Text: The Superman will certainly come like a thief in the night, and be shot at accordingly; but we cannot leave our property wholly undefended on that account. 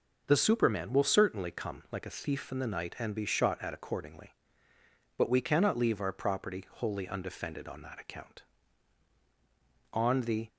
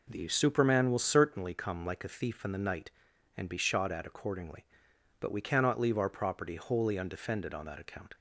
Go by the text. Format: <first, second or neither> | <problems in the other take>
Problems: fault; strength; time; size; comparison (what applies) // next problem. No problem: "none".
second | goes on to say "On the"; from 9.9 s on; 0.56 s long